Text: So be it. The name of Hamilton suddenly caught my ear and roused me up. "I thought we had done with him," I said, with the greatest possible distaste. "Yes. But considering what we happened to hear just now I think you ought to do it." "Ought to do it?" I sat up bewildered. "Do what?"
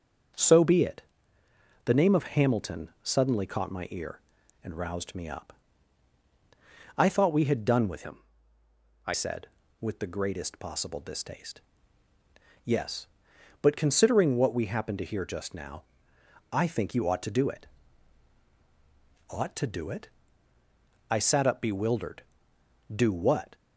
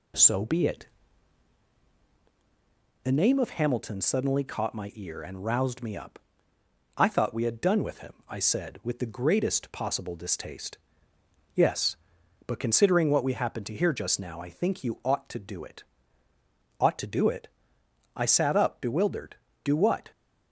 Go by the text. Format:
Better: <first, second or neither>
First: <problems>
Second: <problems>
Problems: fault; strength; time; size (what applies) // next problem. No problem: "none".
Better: second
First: changes voice from "him" to "I"; from 8.0 to 9.1 s; 1.1 s long // pauses between "now" and "I"; noticeable; at 15.8 s; 0.72 s long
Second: none